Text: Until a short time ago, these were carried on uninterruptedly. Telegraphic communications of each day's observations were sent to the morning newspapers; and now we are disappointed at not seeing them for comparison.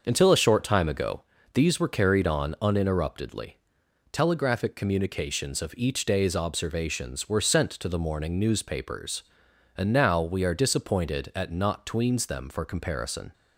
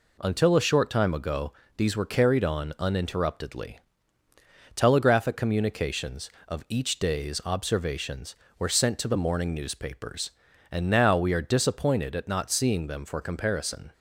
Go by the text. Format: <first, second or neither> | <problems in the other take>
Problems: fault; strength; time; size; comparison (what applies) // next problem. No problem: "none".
second | starts louder than the rest; until 1.0 s; 6.5 dB // says "tweens" for "seeing"; at 11.8 s